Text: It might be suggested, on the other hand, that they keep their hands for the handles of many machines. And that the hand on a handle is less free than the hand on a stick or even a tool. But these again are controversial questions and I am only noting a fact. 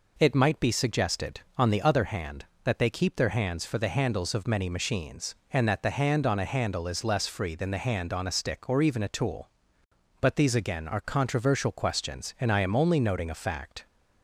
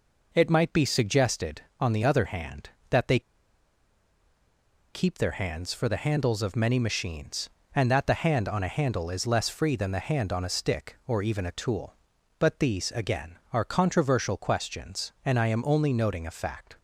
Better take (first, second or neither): first